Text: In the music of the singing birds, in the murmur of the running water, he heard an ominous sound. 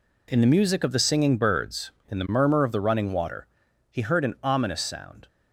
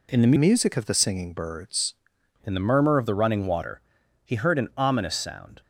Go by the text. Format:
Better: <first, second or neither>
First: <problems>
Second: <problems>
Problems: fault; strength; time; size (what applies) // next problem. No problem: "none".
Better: first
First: none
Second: changes voice from "music" to "birds"; from 0.3 to 1.9 s; 1.6 s long